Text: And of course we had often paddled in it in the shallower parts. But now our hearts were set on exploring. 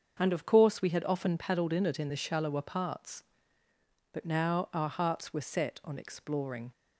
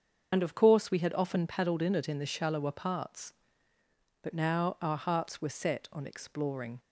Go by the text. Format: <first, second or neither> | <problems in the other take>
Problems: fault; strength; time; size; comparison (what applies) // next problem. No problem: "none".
first | loses the start of "And"; at 0.3 s; 55 ms // starts louder than the rest; until 1.3 s; 6.5 dB; also in the first